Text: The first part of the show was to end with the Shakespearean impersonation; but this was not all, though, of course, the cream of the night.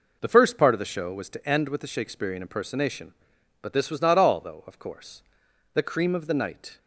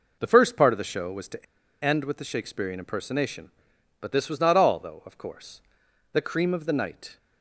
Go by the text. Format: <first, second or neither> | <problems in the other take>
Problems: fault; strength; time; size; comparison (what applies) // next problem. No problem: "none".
first | pauses between "to" and "end"; at 1.4 s; 0.39 s long